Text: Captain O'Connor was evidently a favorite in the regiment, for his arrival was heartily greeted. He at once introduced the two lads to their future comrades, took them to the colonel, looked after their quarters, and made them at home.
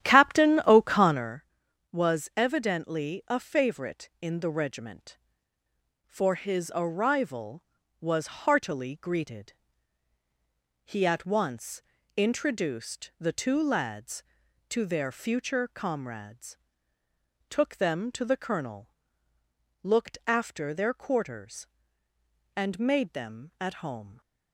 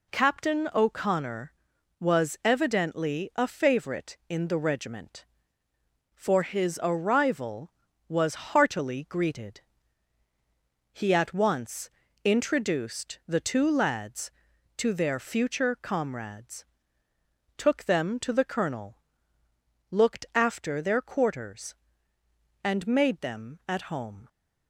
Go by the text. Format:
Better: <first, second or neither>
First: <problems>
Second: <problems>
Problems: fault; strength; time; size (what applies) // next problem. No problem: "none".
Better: second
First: starts louder than the rest; strong; until 1.4 s; 11 dB // pauses between "once" and "introduced"; slight; at 11.8 s; 0.34 s long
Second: pauses between "once" and "introduced"; slight; at 11.8 s; 0.34 s long